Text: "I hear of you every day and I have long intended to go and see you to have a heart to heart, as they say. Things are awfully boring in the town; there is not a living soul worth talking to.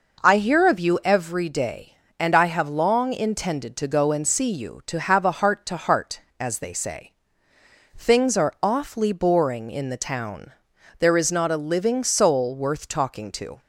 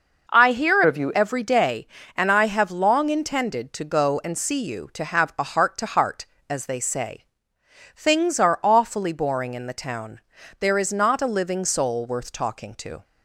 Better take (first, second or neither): first